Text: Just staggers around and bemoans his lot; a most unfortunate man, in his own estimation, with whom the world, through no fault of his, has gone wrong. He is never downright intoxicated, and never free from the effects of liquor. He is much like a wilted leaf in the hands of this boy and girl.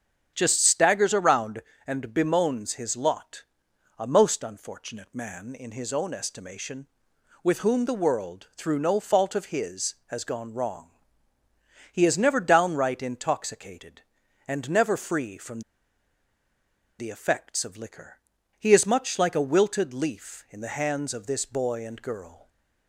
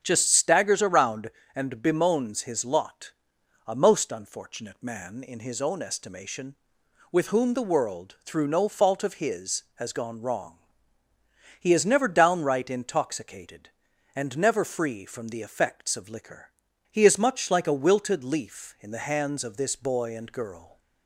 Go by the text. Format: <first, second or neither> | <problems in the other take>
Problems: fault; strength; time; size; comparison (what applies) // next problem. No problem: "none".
second | starts louder than the rest; strong; until 1.3 s; 7.5 dB; strong in the second // pauses between "from" and "the"; strong; at 15.6 s; 1.3 s long // stays silent after the last word; slight; from 22.3 s on; 0.5 s long